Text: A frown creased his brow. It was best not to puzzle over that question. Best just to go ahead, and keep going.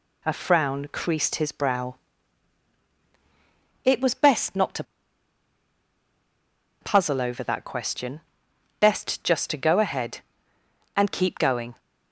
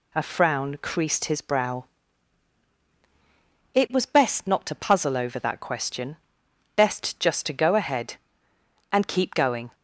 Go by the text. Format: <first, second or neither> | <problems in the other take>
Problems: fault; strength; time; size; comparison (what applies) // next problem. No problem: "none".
second | pauses between "to" and "puzzle"; strong; at 4.8 s; 1.9 s long